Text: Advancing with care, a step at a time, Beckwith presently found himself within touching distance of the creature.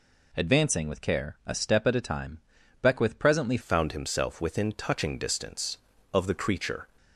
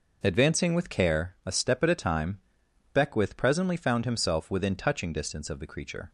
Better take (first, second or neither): second